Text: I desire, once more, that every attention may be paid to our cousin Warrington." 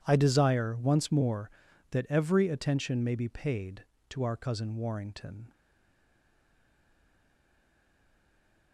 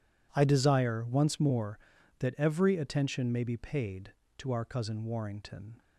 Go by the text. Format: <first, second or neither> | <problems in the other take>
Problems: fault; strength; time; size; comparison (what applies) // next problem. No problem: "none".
second | stays silent after the last word; strong; from 5.5 s on; 3.2 s long